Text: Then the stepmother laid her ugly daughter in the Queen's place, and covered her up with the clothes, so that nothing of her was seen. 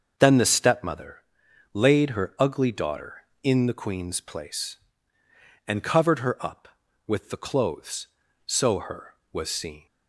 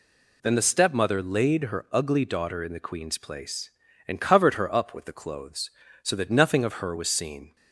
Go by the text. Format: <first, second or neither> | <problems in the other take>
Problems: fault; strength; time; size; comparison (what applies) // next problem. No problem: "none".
second | starts louder than the rest; until 1.7 s; 6.5 dB // pauses between "stepmother" and "laid"; noticeable; at 1.1 s; 0.58 s long // skips "that nothing of"; at 8.7 s